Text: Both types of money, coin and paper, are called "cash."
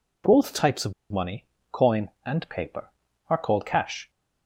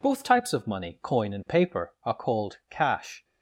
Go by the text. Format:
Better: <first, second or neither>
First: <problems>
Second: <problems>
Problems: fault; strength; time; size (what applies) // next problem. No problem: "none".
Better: second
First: pauses between "of" and "money"; slight; at 0.9 s; 0.18 s long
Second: none